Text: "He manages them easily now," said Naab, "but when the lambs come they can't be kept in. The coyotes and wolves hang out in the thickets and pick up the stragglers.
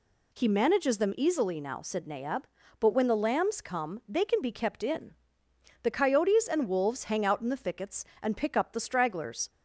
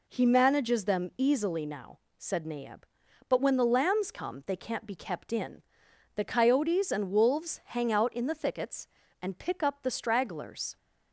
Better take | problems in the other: second | says "can" for "can't"; at 4.2 s

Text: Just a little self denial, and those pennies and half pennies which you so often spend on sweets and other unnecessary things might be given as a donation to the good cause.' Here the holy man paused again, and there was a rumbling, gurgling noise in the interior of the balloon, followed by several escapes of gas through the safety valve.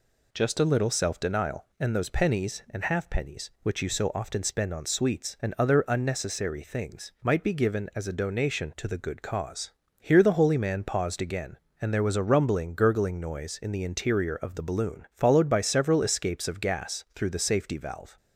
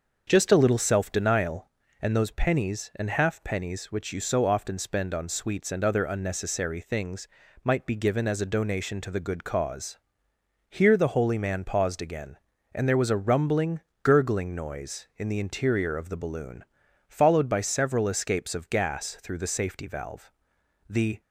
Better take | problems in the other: first | starts louder than the rest; until 1.2 s; 6.5 dB // pauses between "things" and "might"; at 7.2 s; 0.38 s long // goes on to say "The"; slight; from 20.9 s on; 0.30 s long

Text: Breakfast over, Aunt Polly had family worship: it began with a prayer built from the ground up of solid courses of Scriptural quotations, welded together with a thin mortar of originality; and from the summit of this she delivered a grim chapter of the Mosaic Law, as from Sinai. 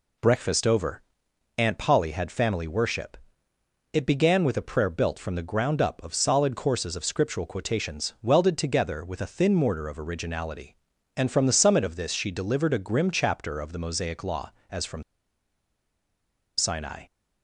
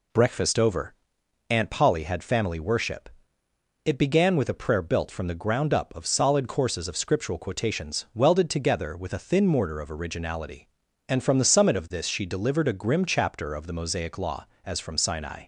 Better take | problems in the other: second | pauses between "from" and "Sinai"; strong; at 15.0 s; 1.5 s long

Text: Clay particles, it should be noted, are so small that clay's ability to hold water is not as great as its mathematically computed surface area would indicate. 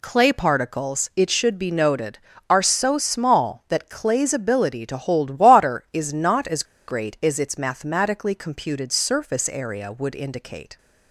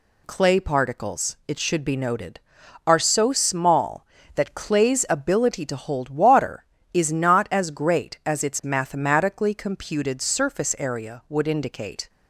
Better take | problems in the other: second | pauses between "as" and "great"; slight; at 6.6 s; 0.23 s long

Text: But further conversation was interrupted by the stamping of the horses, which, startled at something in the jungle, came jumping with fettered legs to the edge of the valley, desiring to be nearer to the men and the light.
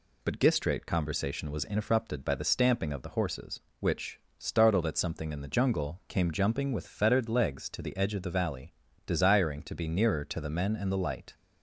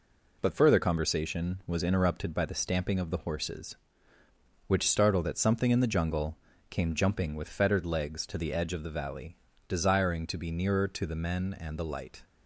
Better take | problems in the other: second | says "gistrate" for "further"; at 0.3 s

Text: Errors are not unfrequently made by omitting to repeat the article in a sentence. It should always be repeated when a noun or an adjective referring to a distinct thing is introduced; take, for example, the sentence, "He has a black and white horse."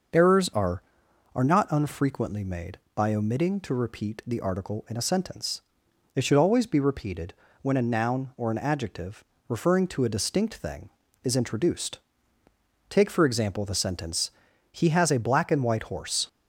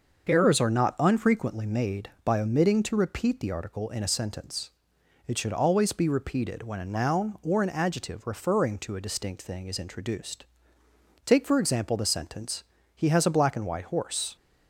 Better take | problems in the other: second | starts louder than the rest; until 1.6 s; 6.5 dB; also in the second // says "are" twice; at 1.3 s // pauses between "repeated" and "when"; slight; at 7.3 s; 0.28 s long // pauses between "adjective" and "referring"; slight; at 9.2 s; 0.24 s long

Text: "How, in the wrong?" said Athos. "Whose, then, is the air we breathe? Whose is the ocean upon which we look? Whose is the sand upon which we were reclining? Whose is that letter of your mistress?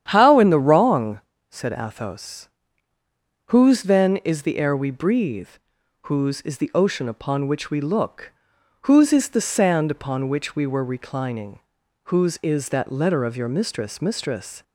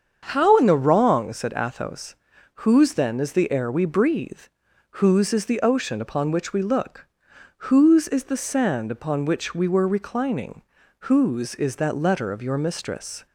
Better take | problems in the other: second | starts louder than the rest; strong; until 1.1 s; 9.5 dB; also in the second // says "mistress" twice; at 14.0 s

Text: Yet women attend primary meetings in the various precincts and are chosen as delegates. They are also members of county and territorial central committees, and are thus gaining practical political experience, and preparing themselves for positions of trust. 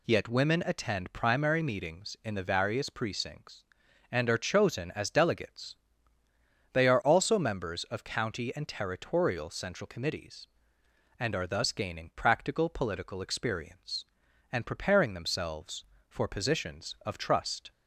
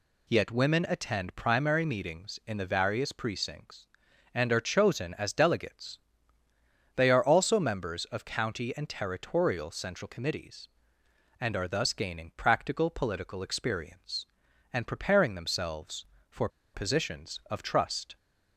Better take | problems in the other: first | pauses between "for" and "positions"; slight; at 16.4 s; 0.26 s long

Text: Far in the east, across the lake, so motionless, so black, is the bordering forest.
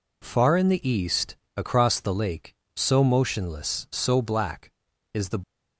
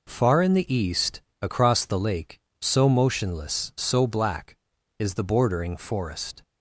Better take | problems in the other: second | stops before "bordering forest"; at 5.4 s

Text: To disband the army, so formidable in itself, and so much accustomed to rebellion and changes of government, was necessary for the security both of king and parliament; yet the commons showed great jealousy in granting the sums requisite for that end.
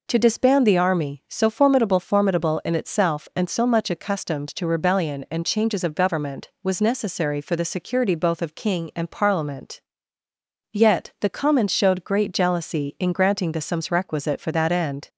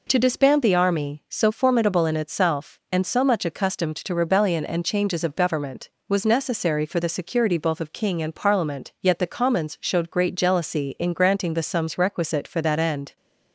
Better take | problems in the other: second | says "formidable" twice; at 1.9 s

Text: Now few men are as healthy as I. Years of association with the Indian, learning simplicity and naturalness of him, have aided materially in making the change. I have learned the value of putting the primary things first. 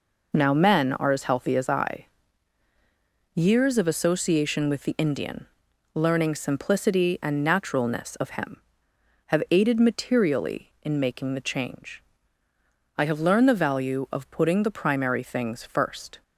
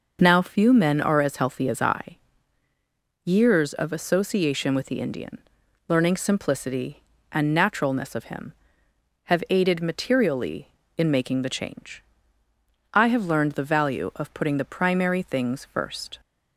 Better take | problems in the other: second | skips "few"; at 0.5 s

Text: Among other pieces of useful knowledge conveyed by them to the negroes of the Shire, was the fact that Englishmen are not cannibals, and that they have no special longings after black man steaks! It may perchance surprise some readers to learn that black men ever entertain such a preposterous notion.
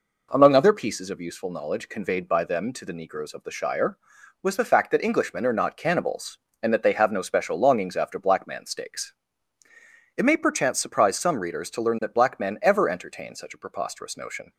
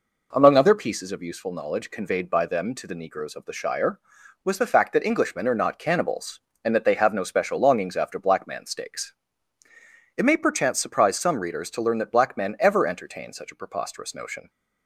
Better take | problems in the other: neither | none

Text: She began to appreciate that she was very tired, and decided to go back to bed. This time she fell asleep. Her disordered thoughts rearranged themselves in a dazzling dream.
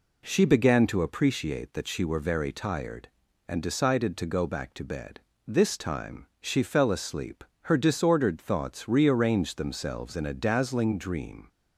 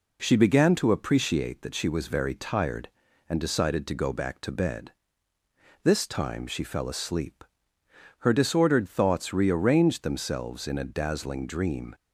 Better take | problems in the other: second | says "were" for "was"; at 2.0 s

